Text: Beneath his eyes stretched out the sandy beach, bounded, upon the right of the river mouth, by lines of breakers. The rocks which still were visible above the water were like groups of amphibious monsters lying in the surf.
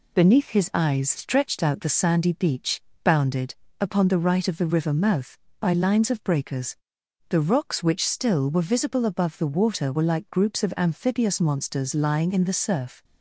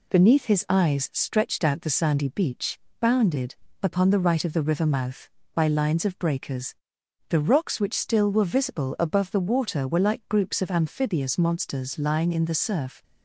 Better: neither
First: none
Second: none

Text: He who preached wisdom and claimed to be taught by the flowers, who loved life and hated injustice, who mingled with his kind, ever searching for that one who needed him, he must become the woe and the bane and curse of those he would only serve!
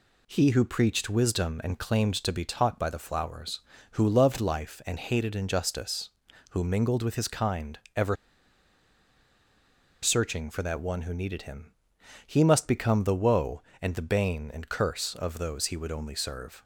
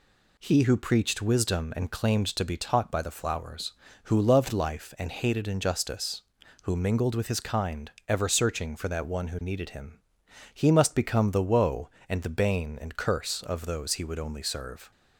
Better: second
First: pauses between "ever" and "searching"; strong; at 8.1 s; 1.8 s long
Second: none

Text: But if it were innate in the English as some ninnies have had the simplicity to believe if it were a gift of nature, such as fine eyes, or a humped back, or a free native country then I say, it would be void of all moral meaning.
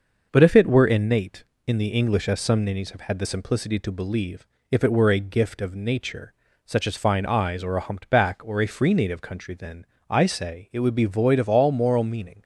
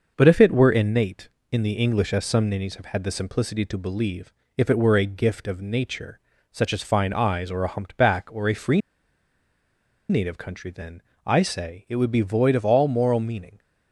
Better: first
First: starts louder than the rest; noticeable; until 1.3 s; 6 dB // pauses between "believe" and "if"; slight; at 4.4 s; 0.24 s long // pauses between "then" and "I"; slight; at 9.8 s; 0.24 s long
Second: starts louder than the rest; noticeable; until 1.1 s; 6 dB // pauses between "believe" and "if"; slight; at 4.3 s; 0.24 s long // pauses between "free" and "native"; strong; at 8.8 s; 1.2 s long // pauses between "then" and "I"; slight; at 11.0 s; 0.24 s long

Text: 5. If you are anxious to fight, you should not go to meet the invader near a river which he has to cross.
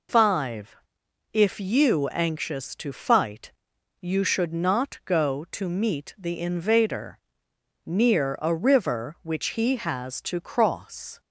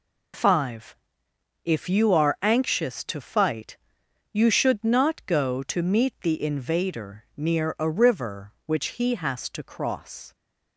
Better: second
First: skips "are"; at 2.0 s // pauses between "invader" and "near"; noticeable; at 7.1 s; 0.66 s long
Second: none

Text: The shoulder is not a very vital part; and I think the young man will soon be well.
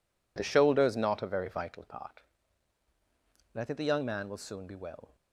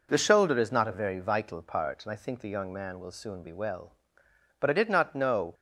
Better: first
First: none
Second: goes on to say "But I did not know"; noticeable; from 4.5 s on; 0.94 s long

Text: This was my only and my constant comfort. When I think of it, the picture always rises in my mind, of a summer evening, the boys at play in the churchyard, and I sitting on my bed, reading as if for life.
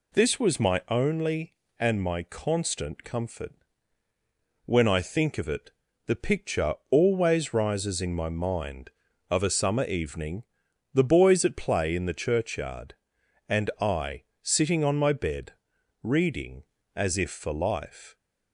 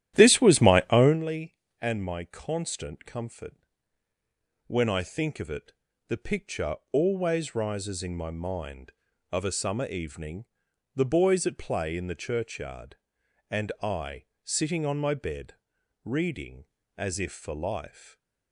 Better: first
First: pauses between "picture" and "always"; slight; at 6.7 s; 0.16 s long // pauses between "I" and "sitting"; slight; at 14.2 s; 0.18 s long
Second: starts louder than the rest; strong; until 1.2 s; 12.5 dB // pauses between "picture" and "always"; slight; at 6.7 s; 0.16 s long // pauses between "I" and "sitting"; slight; at 14.2 s; 0.18 s long // stays silent after the last word; slight; from 17.8 s on; 0.7 s long

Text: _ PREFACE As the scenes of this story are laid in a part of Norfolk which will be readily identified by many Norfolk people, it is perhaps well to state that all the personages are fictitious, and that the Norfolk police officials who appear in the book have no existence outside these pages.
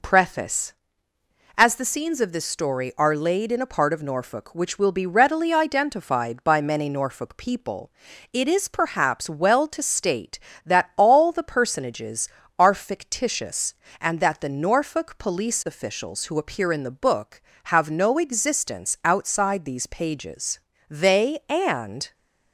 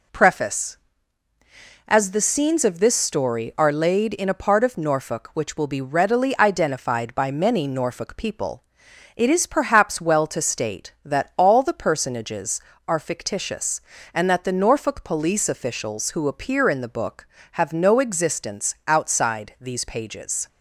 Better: second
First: goes on to say "They and"; noticeable; from 20.8 s on; 1.2 s long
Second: none

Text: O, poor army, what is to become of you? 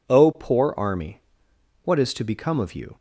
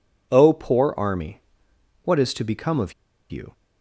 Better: first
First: none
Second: pauses between "of" and "you"; at 2.9 s; 0.39 s long

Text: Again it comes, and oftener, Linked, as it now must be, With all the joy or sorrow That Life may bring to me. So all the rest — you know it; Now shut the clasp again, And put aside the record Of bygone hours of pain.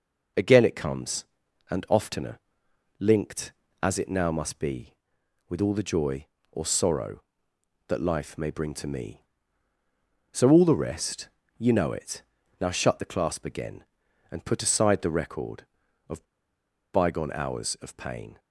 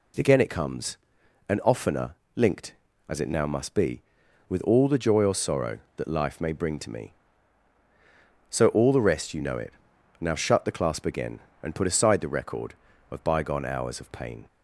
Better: second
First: pauses between "Of" and "bygone"; noticeable; at 16.2 s; 0.69 s long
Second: none

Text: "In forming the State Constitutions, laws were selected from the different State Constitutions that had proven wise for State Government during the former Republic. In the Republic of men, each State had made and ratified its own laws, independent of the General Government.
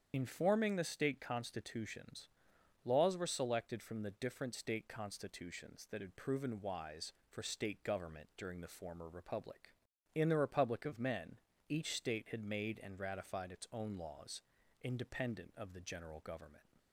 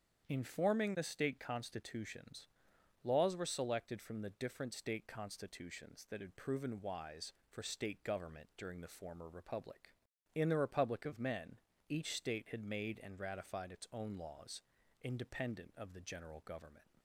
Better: second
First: loses the start of "In"; at 0.1 s; 50 ms // starts louder than the rest; strong; until 1.1 s; 8 dB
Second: starts louder than the rest; strong; until 1.2 s; 8 dB

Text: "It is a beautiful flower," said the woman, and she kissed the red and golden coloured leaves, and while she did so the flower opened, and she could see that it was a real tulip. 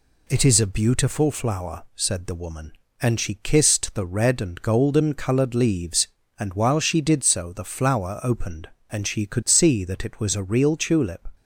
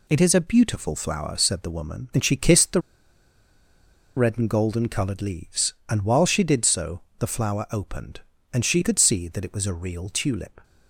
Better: first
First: none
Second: pauses between "the" and "red"; strong; at 2.7 s; 1.3 s long // pauses between "so" and "the"; slight; at 7.0 s; 0.18 s long

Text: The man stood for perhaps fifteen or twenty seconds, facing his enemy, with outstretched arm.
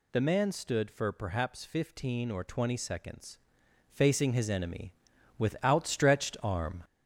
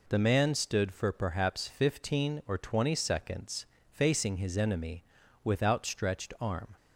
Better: second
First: gets louder; noticeable; throughout; 4.5 dB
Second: none

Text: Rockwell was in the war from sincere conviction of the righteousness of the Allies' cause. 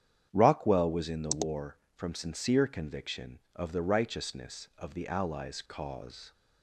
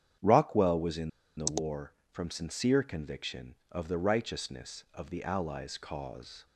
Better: first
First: starts louder than the rest; strong; until 1.3 s; 9 dB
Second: starts louder than the rest; strong; until 1.5 s; 9 dB // pauses between "in" and "the"; slight; at 1.0 s; 0.29 s long

